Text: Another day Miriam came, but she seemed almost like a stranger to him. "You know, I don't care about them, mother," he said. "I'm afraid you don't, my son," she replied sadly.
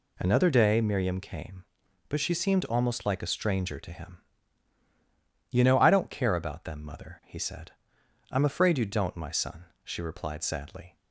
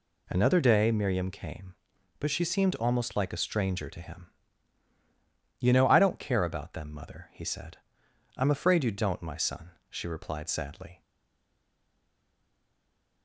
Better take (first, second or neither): first